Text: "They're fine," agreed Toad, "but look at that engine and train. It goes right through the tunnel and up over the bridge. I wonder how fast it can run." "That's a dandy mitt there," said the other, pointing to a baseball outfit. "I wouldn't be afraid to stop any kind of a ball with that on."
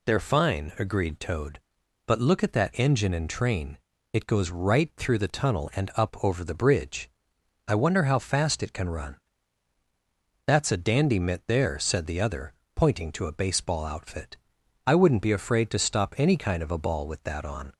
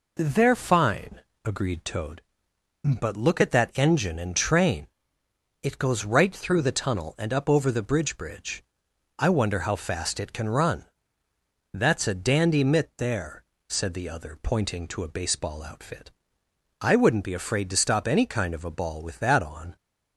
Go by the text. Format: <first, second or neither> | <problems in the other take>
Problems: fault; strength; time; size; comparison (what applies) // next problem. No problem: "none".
first | says "bridge" twice; at 8.1 s